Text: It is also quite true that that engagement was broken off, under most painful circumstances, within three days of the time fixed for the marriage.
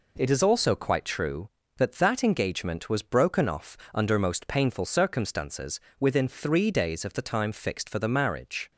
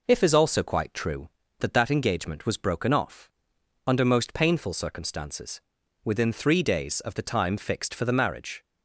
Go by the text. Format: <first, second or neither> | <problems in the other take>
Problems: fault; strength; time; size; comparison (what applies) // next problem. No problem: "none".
first | says "If" for "It"; at 0.0 s